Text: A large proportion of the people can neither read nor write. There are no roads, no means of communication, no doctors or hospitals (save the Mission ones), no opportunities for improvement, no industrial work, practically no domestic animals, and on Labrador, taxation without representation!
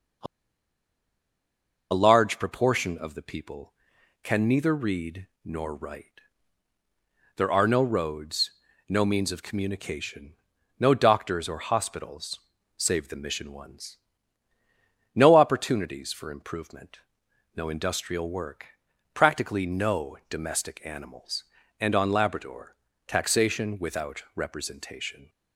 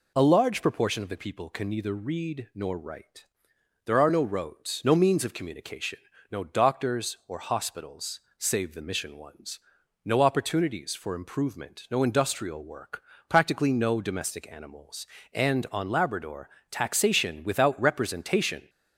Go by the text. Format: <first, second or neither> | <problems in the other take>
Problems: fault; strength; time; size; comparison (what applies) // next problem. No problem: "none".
second | pauses between "A" and "large"; strong; at 0.2 s; 1.6 s long // pauses between "read" and "nor"; slight; at 5.2 s; 0.16 s long